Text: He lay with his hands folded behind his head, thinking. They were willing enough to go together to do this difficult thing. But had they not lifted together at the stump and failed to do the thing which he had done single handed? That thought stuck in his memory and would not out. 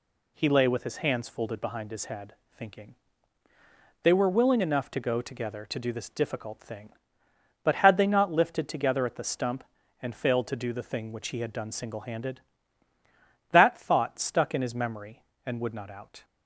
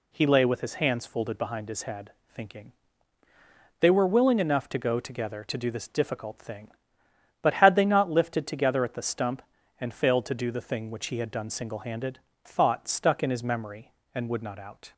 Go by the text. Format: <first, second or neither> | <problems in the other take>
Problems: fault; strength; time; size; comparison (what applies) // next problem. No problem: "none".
first | skips "That"; at 12.3 s